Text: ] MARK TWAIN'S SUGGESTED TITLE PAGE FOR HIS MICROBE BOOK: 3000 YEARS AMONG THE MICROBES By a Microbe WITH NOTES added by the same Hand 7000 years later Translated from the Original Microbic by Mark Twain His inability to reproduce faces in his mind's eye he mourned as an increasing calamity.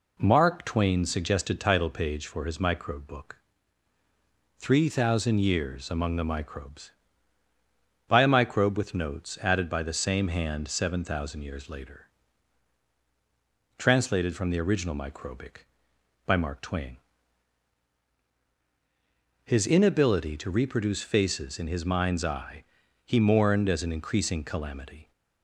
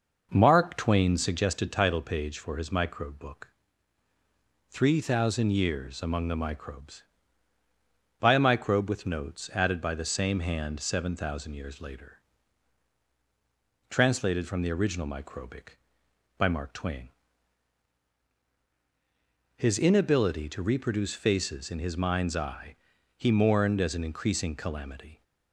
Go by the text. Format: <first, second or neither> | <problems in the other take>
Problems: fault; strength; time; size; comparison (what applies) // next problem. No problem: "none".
first | starts louder than the rest; noticeable; until 1.4 s; 5.5 dB // pauses between "later" and "Translated"; strong; at 12.1 s; 1.7 s long; strong in the first // pauses between "Twain" and "His"; strong; at 17.0 s; 2.4 s long; strong in the first // pauses between "eye" and "he"; at 22.7 s; 0.42 s long; also in the first